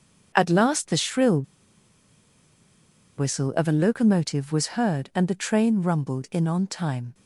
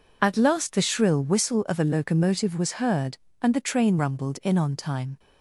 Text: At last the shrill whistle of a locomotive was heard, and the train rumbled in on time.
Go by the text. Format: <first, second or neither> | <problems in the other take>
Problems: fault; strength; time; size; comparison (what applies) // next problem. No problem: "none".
second | starts louder than the rest; strong; until 1.3 s; 7 dB // pauses between "shrill" and "whistle"; strong; at 1.4 s; 1.7 s long